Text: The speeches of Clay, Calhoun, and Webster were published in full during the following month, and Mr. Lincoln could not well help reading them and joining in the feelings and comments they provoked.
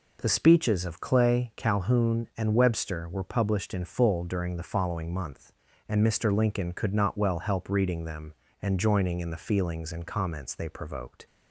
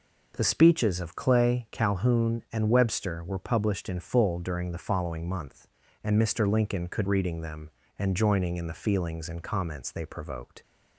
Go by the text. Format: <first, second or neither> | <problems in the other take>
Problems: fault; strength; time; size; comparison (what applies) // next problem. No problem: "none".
first | skips "not well help"; at 7.0 s